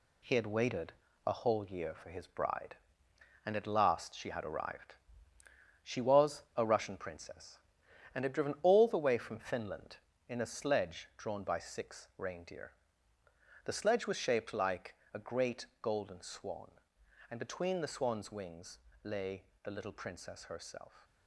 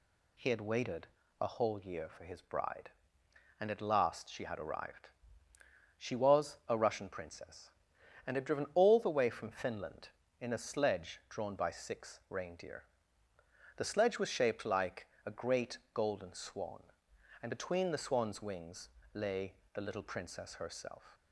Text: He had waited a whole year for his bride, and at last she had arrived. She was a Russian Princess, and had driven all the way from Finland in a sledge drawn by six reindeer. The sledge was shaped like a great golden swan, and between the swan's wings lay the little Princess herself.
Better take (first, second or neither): second